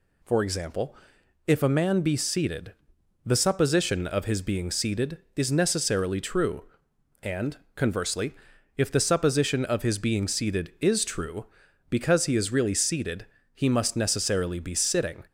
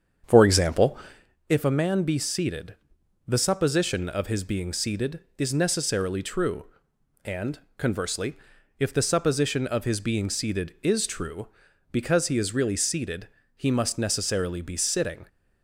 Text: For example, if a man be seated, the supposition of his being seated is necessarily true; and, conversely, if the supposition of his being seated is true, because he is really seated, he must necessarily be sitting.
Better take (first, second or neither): first